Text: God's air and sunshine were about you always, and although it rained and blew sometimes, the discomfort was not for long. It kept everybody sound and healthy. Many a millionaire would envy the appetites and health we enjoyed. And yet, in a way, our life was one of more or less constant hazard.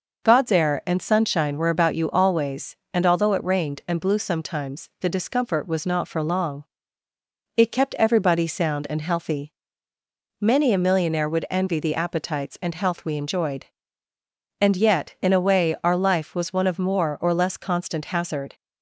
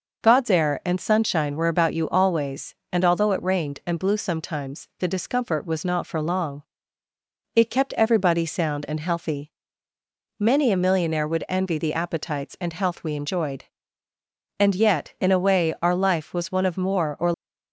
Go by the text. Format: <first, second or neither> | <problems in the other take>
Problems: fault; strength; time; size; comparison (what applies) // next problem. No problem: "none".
first | stops before "less constant hazard"; at 17.3 s